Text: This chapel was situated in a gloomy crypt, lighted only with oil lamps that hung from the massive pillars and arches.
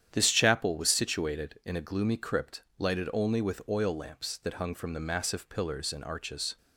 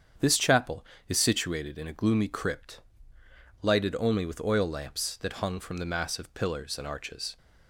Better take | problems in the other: first | starts louder than the rest; strong; until 1.4 s; 8 dB; strong in the first // says "is" for "was"; at 1.0 s

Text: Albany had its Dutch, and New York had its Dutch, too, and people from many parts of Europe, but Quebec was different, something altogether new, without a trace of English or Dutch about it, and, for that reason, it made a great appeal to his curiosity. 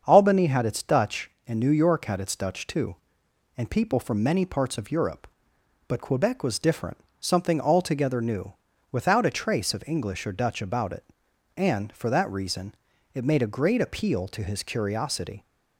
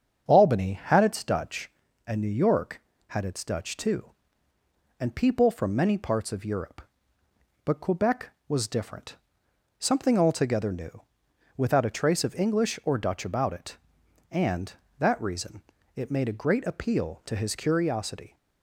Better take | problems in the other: first | starts louder than the rest; strong; until 1.2 s; 7.5 dB; also in the first // skips "for"; at 14.8 s

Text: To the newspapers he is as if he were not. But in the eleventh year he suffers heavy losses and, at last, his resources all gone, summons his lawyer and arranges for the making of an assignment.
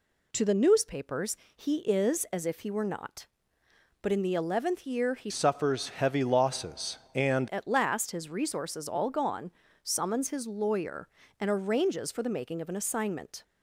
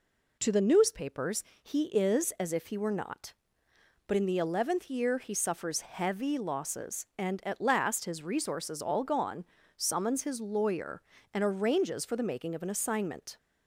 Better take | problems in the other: second | pauses between "newspapers" and "he"; slight; at 1.3 s; 0.18 s long; slight in the second // changes voice from "suffers" to "and"; from 5.2 to 7.4 s; 2.2 s long

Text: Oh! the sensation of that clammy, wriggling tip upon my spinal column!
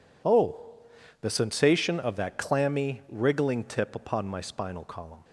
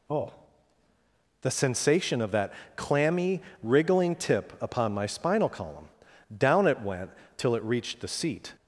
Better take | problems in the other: first | pauses between "that" and "clammy"; slight; at 2.5 s; 0.24 s long // goes on to say "Down it went till it reached the seat"; strong; from 6.3 s on; 2.1 s long

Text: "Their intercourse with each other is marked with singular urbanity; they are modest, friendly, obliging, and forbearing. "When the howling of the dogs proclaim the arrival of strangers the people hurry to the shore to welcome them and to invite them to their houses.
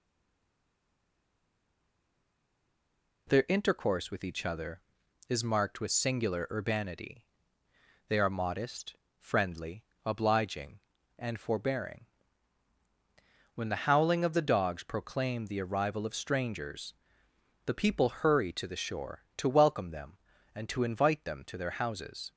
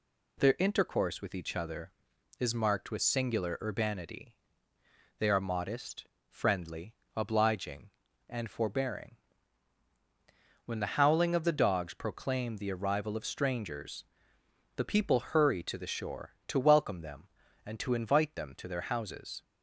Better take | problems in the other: second | stays silent before the first word; strong; until 3.2 s; 3.2 s long // pauses between "strangers" and "the"; noticeable; at 16.9 s; 0.72 s long; noticeable in the second

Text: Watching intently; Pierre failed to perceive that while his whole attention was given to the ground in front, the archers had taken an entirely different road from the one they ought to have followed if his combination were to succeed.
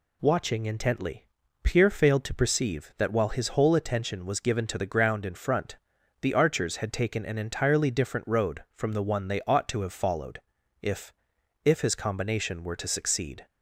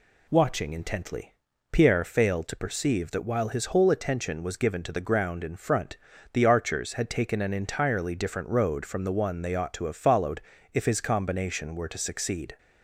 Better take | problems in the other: second | pauses between "followed" and "if"; at 10.4 s; 0.40 s long; slight in the second // says "if" twice; at 11.6 s

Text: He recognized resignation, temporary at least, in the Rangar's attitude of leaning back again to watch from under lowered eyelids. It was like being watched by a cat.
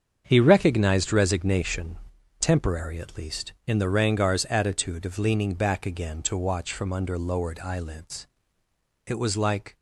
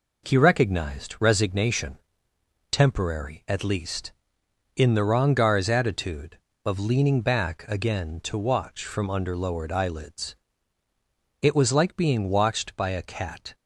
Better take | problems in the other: second | starts louder than the rest; strong; until 1.2 s; 7.5 dB // stops before "being watched by a cat"; at 9.7 s

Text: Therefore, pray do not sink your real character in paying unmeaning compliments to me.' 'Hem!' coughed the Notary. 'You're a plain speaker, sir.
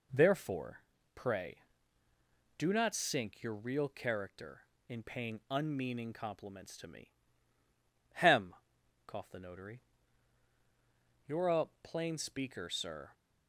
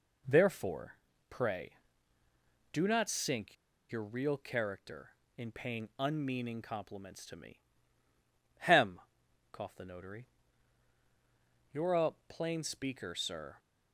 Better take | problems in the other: first | pauses between "sink" and "your"; slight; at 3.5 s; 0.35 s long // pauses between "a" and "plain"; slight; at 12.1 s; 0.16 s long; slight in the first

